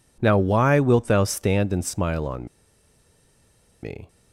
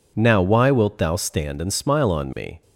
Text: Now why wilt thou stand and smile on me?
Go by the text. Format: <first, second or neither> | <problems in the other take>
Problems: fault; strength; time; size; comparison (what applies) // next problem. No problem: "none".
second | pauses between "on" and "me"; strong; at 2.4 s; 1.3 s long